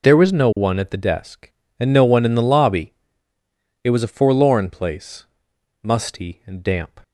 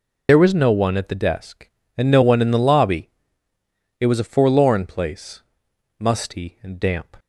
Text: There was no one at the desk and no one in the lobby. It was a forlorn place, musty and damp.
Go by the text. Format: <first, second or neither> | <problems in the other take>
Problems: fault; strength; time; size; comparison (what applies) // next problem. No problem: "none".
first | loses the start of "There"; at 0.2 s; 40 ms